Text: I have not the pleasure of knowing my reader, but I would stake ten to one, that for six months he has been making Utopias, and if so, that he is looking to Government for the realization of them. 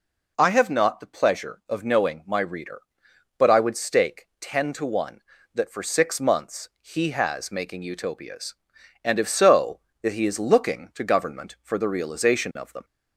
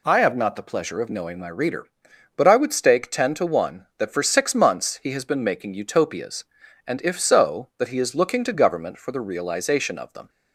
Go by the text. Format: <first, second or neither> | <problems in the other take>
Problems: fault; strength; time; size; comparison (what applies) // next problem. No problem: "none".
second | skips "been"; at 7.5 s